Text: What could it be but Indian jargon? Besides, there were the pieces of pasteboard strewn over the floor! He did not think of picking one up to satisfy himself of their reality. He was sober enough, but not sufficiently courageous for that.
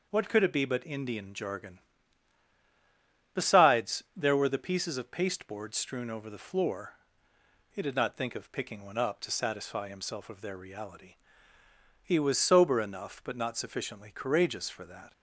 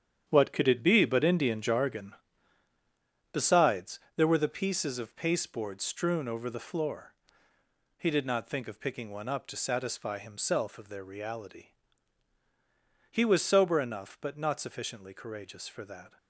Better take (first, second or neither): first